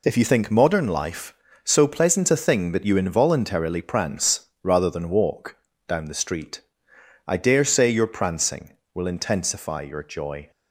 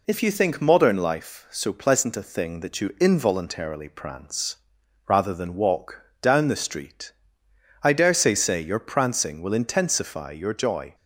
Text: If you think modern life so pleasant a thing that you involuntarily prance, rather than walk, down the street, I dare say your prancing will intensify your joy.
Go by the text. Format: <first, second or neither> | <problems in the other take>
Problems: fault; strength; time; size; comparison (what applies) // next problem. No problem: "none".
first | says "say" twice; at 8.3 s